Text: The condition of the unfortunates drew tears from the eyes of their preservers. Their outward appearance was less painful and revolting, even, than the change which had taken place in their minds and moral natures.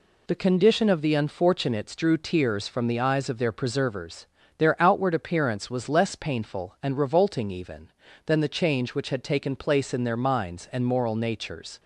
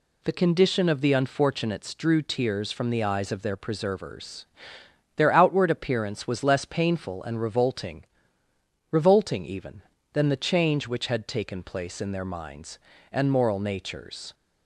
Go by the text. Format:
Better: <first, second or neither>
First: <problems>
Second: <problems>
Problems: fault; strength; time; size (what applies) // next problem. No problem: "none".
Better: first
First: none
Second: says "revolting" twice; at 8.9 s